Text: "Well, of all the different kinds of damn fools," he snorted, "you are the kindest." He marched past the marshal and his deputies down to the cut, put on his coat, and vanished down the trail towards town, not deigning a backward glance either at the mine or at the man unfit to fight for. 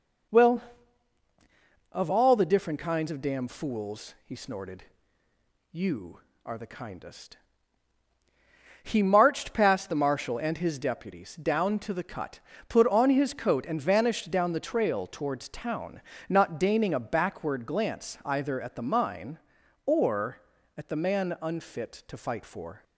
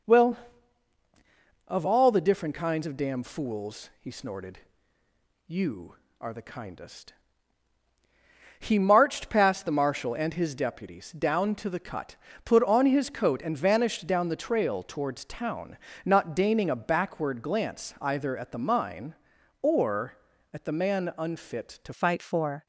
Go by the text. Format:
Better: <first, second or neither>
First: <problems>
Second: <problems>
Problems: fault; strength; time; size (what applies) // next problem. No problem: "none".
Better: first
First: none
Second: changes voice at "fight"; from 21.9 s on; 0.7 s long